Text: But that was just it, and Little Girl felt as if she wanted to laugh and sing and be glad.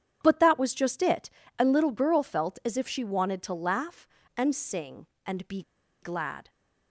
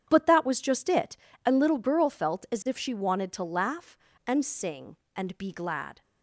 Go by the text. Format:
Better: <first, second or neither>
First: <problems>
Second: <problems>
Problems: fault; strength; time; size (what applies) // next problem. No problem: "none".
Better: second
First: starts louder than the rest; strong; until 1.2 s; 9 dB // pauses between "be" and "glad"; at 5.6 s; 0.41 s long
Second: starts louder than the rest; strong; until 1.1 s; 9 dB